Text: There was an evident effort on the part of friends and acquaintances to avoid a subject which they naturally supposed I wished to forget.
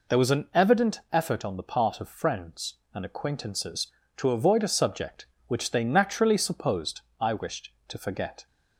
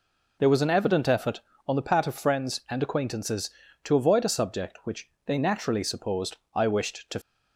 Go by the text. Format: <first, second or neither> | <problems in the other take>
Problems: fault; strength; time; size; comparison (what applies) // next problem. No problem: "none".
first | pauses between "which" and "they"; slight; at 5.0 s; 0.18 s long // pauses between "supposed" and "I"; slight; at 6.3 s; 0.16 s long; slight in the first // stops before "forget"; at 7.2 s